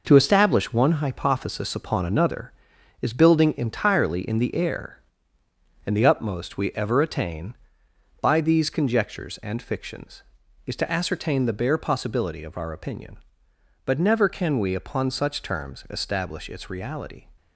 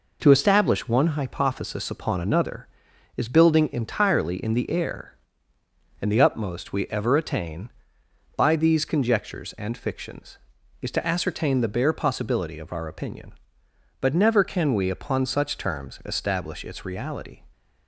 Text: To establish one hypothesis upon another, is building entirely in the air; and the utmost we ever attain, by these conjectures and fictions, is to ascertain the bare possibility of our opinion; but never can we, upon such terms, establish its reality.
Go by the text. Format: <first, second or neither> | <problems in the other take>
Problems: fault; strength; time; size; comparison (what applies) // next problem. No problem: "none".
second | gets quieter; throughout; 7 dB